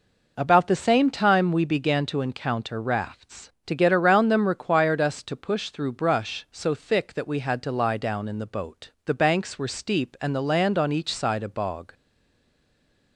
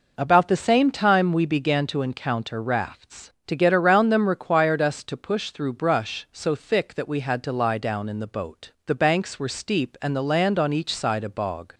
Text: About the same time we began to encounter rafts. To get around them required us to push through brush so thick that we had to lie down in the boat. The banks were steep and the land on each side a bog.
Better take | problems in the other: second | stays silent after the last word; noticeable; from 11.9 s on; 1.2 s long

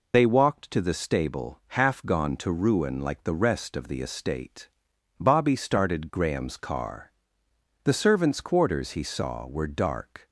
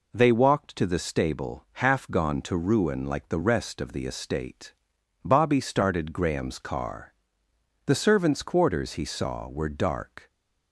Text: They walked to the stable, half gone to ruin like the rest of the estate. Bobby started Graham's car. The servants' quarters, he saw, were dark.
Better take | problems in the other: second | loses the start of "They"; at 0.1 s; 80 ms

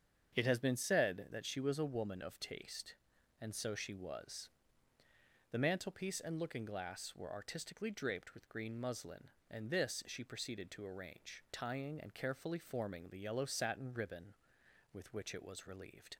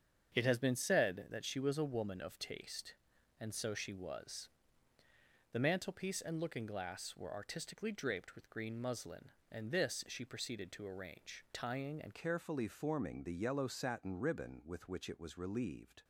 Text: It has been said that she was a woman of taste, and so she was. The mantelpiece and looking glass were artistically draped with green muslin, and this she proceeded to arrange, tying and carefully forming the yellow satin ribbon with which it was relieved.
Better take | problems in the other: first | starts louder than the rest; strong; until 1.3 s; 7.5 dB; strong in the first // changes voice at "carefully"; from 12.1 s on; 3.9 s long

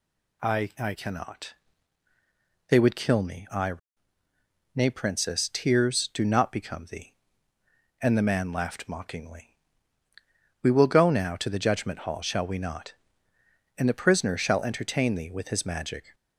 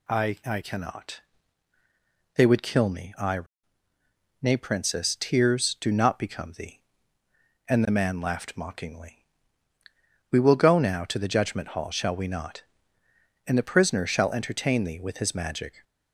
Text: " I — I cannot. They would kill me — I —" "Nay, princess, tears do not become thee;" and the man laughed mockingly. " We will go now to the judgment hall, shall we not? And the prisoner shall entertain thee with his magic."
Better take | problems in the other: neither | none

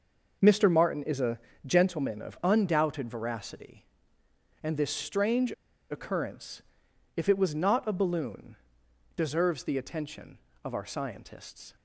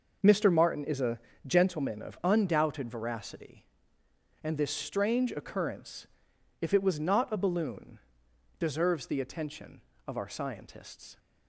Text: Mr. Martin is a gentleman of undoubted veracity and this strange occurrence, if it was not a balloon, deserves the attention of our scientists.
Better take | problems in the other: second | pauses between "a" and "gentleman"; slight; at 1.3 s; 0.28 s long; slight in the second // pauses between "strange" and "occurrence"; at 5.5 s; 0.38 s long

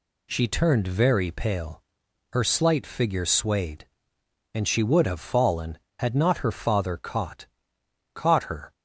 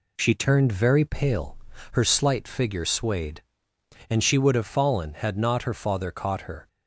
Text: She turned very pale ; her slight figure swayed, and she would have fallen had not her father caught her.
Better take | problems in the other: second | says "caught" twice; at 8.1 s

